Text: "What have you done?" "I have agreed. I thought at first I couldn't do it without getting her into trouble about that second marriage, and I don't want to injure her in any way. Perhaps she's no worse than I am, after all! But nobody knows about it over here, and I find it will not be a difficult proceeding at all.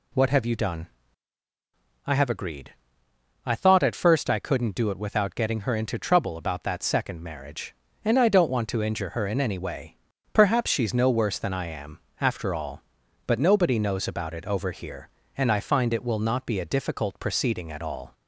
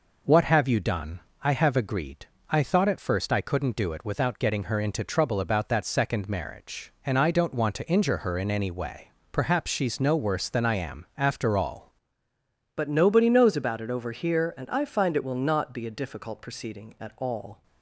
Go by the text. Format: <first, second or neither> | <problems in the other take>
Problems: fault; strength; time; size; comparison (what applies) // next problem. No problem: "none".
first | changes voice at "But"; from 12.7 s on; 4.9 s long